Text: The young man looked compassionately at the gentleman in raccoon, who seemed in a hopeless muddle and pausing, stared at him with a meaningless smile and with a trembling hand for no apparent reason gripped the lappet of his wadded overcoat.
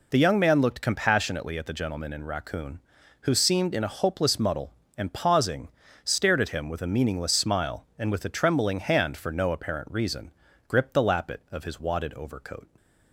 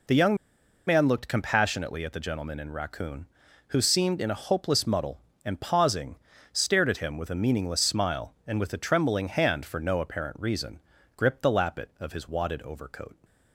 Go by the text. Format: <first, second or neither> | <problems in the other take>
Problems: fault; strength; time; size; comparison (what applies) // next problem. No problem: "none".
first | pauses between "young" and "man"; noticeable; at 0.3 s; 0.52 s long // pauses between "reason" and "gripped"; at 10.7 s; 0.38 s long; also in the first